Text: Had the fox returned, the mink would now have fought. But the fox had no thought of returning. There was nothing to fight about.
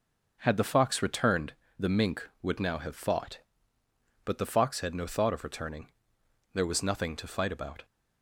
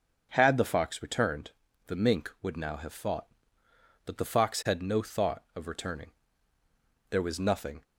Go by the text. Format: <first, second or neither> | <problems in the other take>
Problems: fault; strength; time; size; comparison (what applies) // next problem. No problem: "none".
first | starts louder than the rest; until 1.3 s; 6.5 dB // stops before "to fight about"; at 7.8 s